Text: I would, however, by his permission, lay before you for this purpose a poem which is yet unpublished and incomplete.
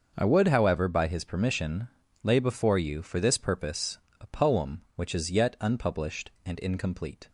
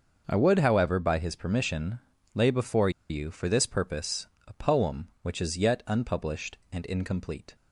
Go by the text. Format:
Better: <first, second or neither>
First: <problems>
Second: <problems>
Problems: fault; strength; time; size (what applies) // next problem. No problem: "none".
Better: first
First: starts louder than the rest; until 1.1 s; 6.5 dB // pauses between "purpose" and "a"; slight; at 3.9 s; 0.20 s long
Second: starts louder than the rest; until 1.3 s; 6.5 dB // pauses between "before" and "you"; slight; at 2.8 s; 0.20 s long // pauses between "purpose" and "a"; slight; at 4.2 s; 0.18 s long